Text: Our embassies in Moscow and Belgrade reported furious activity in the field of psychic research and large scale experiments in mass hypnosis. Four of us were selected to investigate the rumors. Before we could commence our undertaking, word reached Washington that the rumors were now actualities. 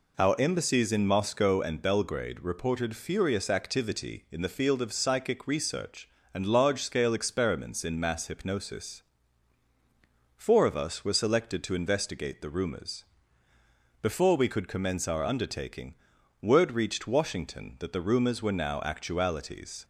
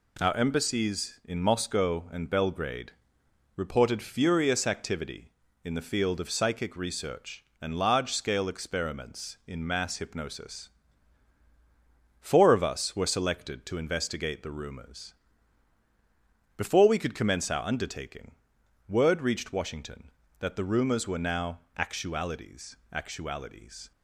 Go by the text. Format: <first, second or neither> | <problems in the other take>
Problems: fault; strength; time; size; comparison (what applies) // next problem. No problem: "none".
first | pauses between "Belgrade" and "reported"; noticeable; at 2.9 s; 0.62 s long // pauses between "now" and "actualities"; slight; at 21.5 s; 0.18 s long // says "actualities" twice; at 22.9 s